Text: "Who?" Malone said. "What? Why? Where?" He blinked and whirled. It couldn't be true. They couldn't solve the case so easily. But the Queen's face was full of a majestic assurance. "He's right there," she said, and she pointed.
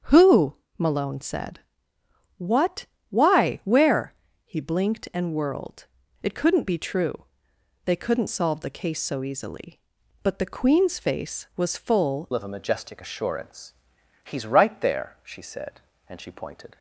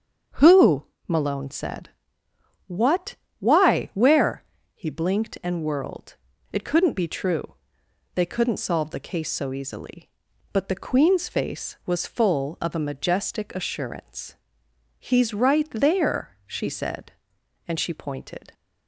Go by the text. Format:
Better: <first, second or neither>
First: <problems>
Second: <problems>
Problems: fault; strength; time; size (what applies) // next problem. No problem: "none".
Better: second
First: starts louder than the rest; strong; until 1.2 s; 7 dB // changes voice at "of"; from 12.3 s on; 4.4 s long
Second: starts louder than the rest; strong; until 1.5 s; 7 dB